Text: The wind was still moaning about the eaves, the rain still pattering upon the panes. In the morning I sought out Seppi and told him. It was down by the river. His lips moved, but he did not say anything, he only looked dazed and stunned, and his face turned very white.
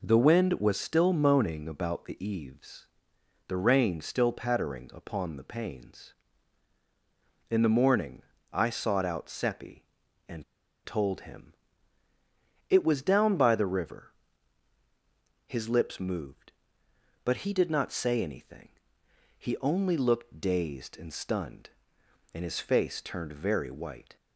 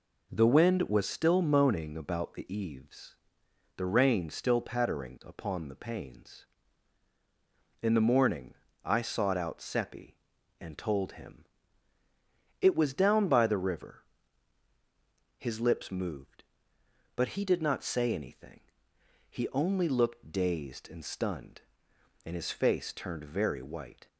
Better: second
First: pauses between "morning" and "I"; slight; at 8.2 s; 0.28 s long // pauses between "and" and "told"; at 10.4 s; 0.41 s long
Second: pauses between "morning" and "I"; slight; at 8.5 s; 0.28 s long

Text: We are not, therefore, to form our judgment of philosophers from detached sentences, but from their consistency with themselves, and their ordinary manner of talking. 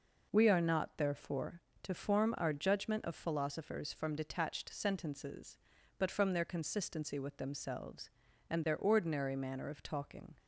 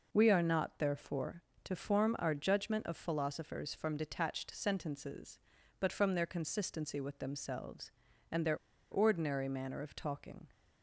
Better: first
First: none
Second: pauses between "their" and "ordinary"; slight; at 8.5 s; 0.34 s long

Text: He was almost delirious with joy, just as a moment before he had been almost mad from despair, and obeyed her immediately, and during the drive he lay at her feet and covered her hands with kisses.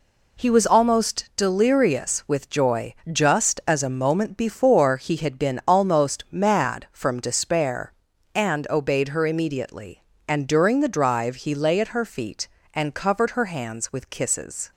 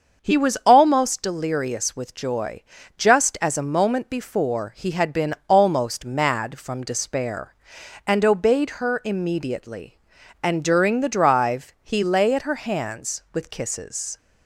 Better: first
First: none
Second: starts louder than the rest; until 1.2 s; 6.5 dB // skips "her feet and covered"; at 12.4 s

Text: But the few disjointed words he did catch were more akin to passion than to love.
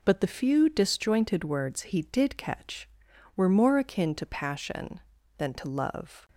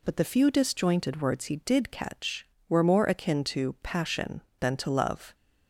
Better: neither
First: none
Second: none

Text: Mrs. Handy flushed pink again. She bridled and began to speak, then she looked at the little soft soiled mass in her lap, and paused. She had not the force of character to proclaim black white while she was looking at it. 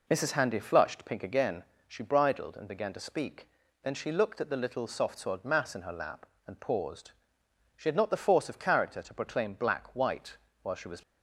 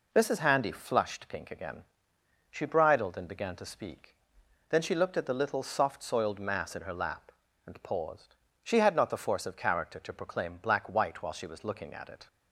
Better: second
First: pauses between "white" and "while"; slight; at 10.3 s; 0.26 s long // stops before "looking at it"; at 11.0 s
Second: none

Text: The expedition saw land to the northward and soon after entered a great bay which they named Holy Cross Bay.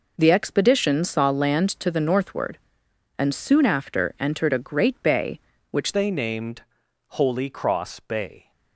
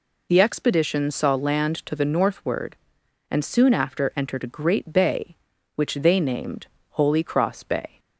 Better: second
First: changes voice at "they"; from 5.9 s on; 2.6 s long // pauses between "named" and "Holy"; noticeable; at 6.6 s; 0.48 s long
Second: pauses between "named" and "Holy"; slight; at 6.6 s; 0.24 s long

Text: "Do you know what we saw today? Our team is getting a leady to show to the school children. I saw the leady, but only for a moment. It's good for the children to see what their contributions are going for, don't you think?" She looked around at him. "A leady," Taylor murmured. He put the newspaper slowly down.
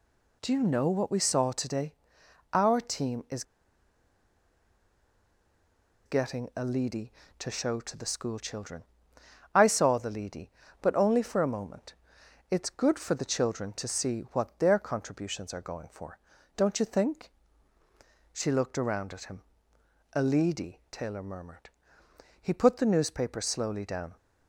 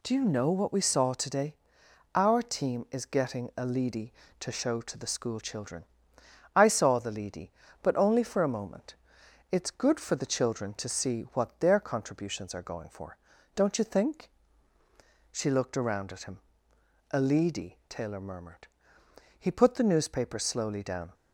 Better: second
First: pauses between "is" and "getting"; strong; at 3.4 s; 2.6 s long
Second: none

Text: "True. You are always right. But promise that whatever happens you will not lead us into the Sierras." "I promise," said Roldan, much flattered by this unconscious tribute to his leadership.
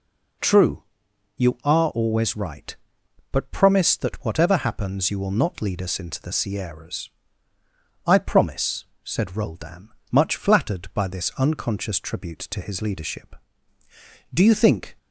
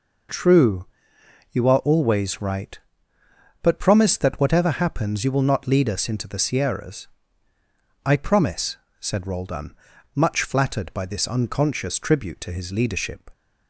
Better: second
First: goes on to say "Do you think"; noticeable; from 14.3 s on; 0.64 s long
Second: none

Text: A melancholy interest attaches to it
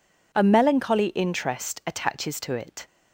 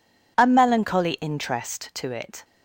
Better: first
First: none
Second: skips "attaches"; at 1.9 s

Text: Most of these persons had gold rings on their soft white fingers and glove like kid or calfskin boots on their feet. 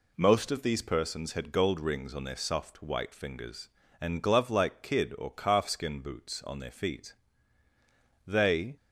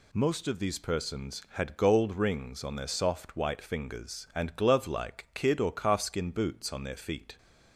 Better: second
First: goes on to say "They"; from 8.2 s on; 0.50 s long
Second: none

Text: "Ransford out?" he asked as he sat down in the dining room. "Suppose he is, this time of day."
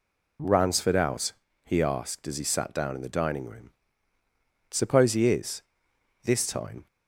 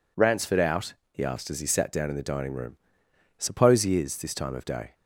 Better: second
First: stops before "of day"; at 6.8 s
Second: none

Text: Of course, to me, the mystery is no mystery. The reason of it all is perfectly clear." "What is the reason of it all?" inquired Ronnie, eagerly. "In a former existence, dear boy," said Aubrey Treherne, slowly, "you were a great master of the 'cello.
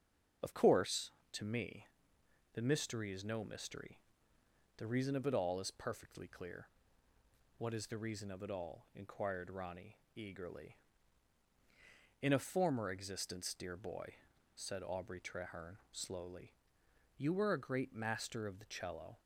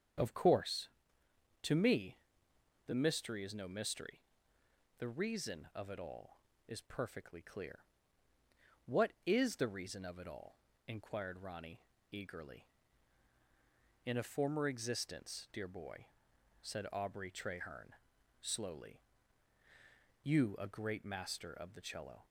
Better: first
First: starts louder than the rest; until 1.6 s; 7 dB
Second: starts louder than the rest; strong; until 1.9 s; 8 dB // skips "were"; at 20.5 s

